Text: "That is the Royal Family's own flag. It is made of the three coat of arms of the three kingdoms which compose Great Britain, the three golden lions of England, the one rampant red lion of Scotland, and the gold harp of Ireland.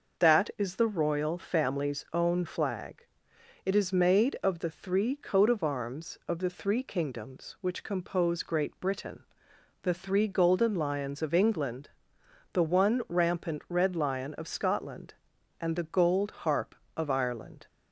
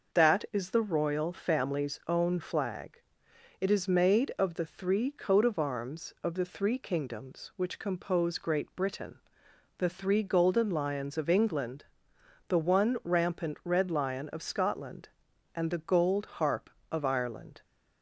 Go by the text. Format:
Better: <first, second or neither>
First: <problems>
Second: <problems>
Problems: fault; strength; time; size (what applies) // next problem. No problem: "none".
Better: neither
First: pauses between "gold" and "harp"; slight; at 16.3 s; 0.16 s long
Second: pauses between "gold" and "harp"; slight; at 16.2 s; 0.16 s long